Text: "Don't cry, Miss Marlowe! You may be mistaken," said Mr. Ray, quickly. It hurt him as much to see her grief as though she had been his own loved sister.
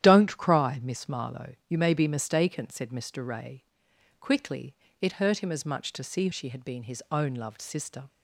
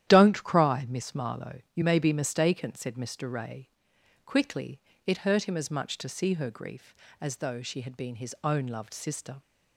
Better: second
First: starts louder than the rest; strong; until 1.0 s; 11 dB // skips "her grief as though"; at 6.3 s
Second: starts louder than the rest; strong; until 1.1 s; 11.5 dB

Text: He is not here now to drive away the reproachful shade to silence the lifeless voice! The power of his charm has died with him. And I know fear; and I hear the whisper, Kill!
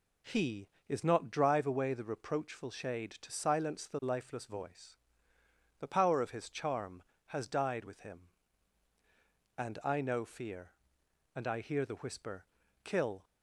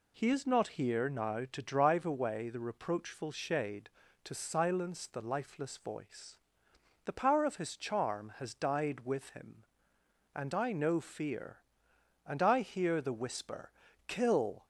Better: second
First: skips "here now to"; at 1.2 s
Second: none

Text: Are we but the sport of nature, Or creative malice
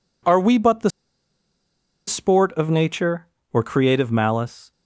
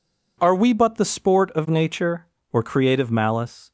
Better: second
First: pauses between "the" and "sport"; at 0.8 s; 1.1 s long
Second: none

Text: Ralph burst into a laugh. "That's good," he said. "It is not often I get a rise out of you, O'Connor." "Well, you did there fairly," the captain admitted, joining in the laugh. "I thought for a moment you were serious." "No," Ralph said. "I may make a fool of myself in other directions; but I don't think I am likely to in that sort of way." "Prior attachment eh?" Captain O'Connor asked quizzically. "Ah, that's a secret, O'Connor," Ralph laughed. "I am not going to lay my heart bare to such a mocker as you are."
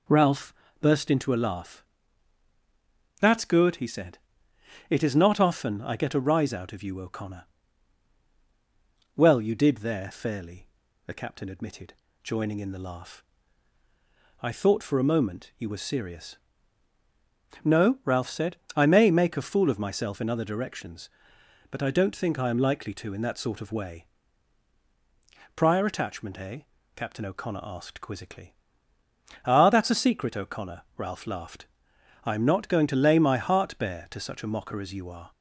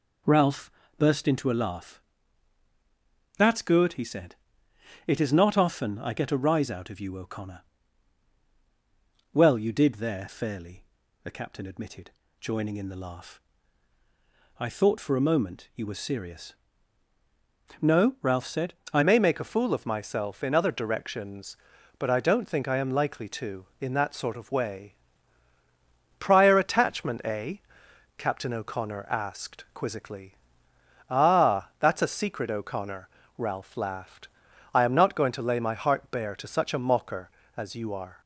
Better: first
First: pauses between "Ralph" and "burst"; slight; at 0.5 s; 0.26 s long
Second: pauses between "Ralph" and "burst"; slight; at 0.7 s; 0.26 s long // changes voice at "may"; from 19.0 s on; 19.2 s long

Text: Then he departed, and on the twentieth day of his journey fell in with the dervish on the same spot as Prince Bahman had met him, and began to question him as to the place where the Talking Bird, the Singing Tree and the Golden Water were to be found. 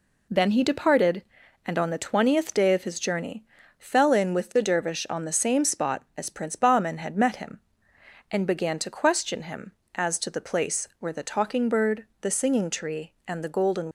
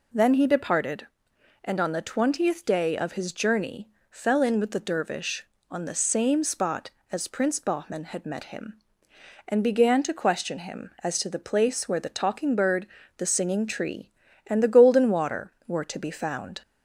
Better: second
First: pauses between "journey" and "fell"; slight; at 3.4 s; 0.34 s long // stops before "Water were to be found"; at 13.8 s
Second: pauses between "journey" and "fell"; slight; at 3.8 s; 0.22 s long

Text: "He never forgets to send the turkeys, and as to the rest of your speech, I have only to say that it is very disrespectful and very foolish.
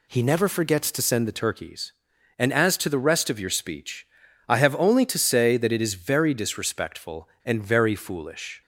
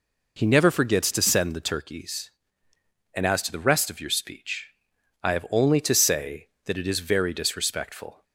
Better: first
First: none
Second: stops before "and very foolish"; at 8.2 s

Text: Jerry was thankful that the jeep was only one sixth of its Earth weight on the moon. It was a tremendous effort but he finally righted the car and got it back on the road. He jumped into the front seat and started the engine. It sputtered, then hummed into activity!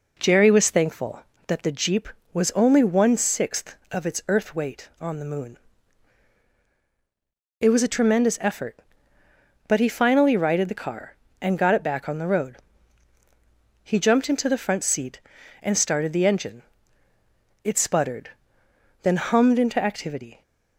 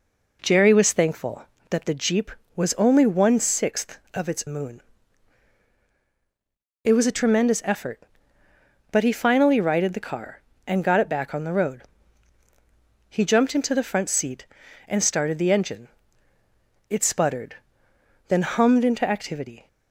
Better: first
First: none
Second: skips "Earth weight on the"; at 4.4 s

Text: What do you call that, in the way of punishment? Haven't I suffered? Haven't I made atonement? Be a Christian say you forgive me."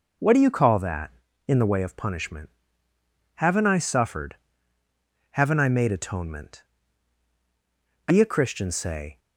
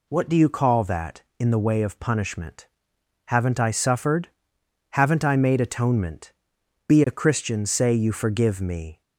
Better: second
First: stops before "you forgive me"; at 9.1 s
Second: none

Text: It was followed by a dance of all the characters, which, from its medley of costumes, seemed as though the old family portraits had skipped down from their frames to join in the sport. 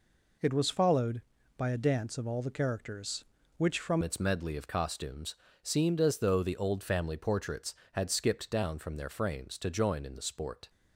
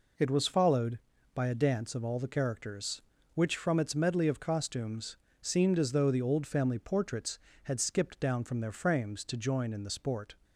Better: second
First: changes voice at "its"; from 4.0 s on; 6.6 s long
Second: none

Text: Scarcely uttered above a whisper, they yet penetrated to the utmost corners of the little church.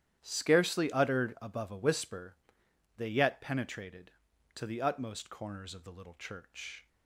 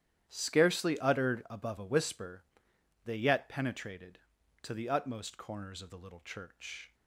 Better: neither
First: starts louder than the rest; strong; until 1.2 s; 11 dB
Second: starts louder than the rest; strong; until 1.2 s; 11 dB

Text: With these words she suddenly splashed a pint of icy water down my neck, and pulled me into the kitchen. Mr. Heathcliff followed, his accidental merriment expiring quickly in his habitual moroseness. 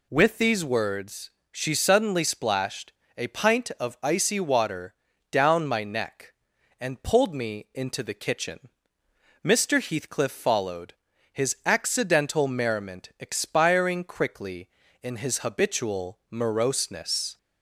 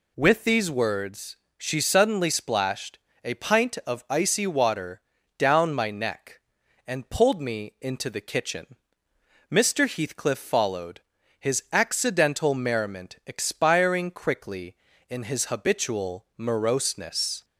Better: neither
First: pauses between "words" and "she"; slight; at 1.3 s; 0.22 s long // pauses between "splashed" and "a"; slight; at 2.9 s; 0.25 s long // pauses between "water" and "down"; at 4.9 s; 0.38 s long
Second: pauses between "words" and "she"; slight; at 1.3 s; 0.22 s long // pauses between "splashed" and "a"; slight; at 2.9 s; 0.25 s long // pauses between "water" and "down"; at 5.0 s; 0.38 s long

